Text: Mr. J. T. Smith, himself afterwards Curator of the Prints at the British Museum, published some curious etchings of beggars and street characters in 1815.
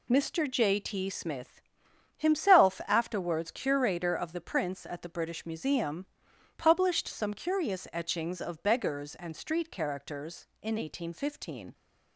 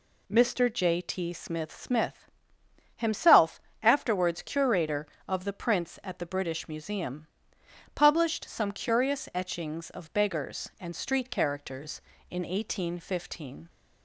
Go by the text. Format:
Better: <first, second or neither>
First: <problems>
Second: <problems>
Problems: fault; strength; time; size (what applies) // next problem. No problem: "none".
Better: first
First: none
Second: says "Smith" twice; at 1.7 s // pauses between "himself" and "afterwards"; slight; at 3.6 s; 0.22 s long